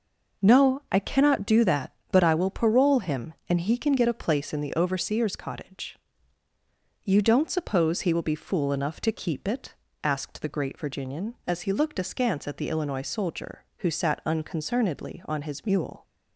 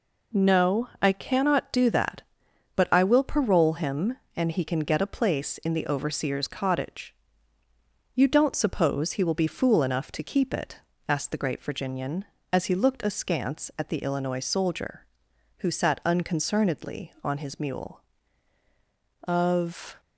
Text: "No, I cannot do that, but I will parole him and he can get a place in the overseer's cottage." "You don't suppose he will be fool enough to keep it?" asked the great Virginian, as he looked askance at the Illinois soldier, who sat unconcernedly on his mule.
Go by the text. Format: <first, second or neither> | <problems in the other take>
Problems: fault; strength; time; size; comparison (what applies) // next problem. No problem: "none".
first | goes on to say "Of"; noticeable; from 19.2 s on; 0.76 s long